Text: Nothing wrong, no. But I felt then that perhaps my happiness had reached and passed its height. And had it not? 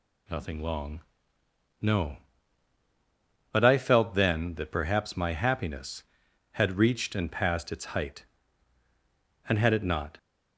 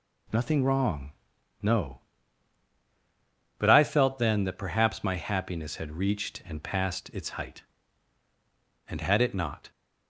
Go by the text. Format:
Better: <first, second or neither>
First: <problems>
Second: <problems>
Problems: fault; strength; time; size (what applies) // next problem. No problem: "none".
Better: second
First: says "long" for "wrong"; at 0.6 s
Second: none